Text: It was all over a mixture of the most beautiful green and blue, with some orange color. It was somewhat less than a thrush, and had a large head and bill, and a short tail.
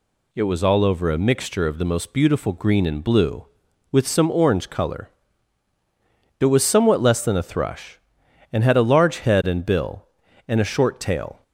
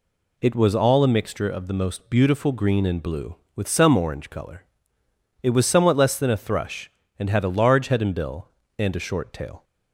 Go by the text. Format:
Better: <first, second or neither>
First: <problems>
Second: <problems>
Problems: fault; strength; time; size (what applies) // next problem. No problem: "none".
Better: first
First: none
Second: skips "over"; at 1.0 s